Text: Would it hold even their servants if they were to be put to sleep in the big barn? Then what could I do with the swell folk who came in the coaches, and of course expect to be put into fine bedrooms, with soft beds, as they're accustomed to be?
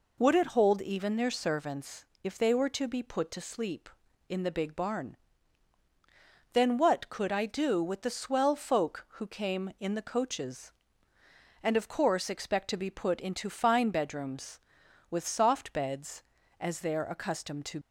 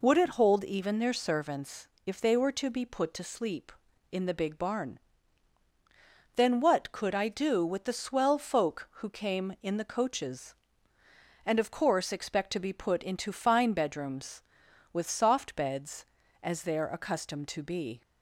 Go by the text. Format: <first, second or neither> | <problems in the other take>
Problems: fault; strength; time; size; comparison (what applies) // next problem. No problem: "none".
second | pauses between "servants" and "if"; slight; at 2.0 s; 0.22 s long; slight in the second // stops before "be"; at 17.8 s